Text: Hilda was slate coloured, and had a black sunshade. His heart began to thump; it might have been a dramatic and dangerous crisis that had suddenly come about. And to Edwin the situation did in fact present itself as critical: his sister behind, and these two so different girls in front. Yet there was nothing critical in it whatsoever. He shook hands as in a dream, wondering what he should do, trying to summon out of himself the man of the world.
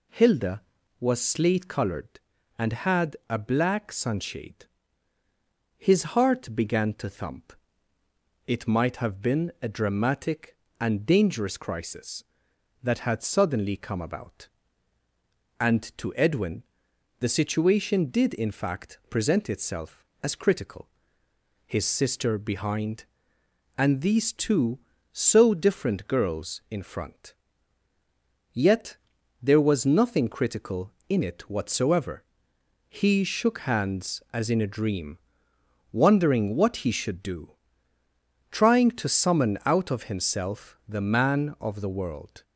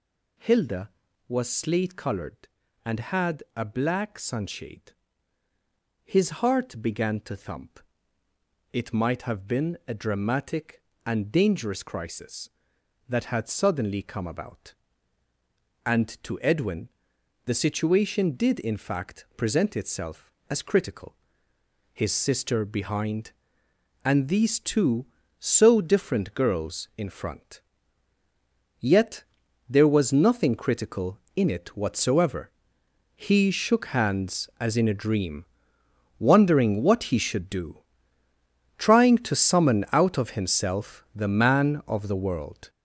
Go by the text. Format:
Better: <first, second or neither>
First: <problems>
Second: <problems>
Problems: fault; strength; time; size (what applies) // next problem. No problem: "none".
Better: first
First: pauses between "Edwin" and "the"; noticeable; at 16.6 s; 0.56 s long // pauses between "Yet" and "there"; at 28.9 s; 0.44 s long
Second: gets louder; strong; throughout; 8.5 dB // pauses between "Edwin" and "the"; noticeable; at 16.8 s; 0.56 s long // pauses between "Yet" and "there"; at 29.2 s; 0.44 s long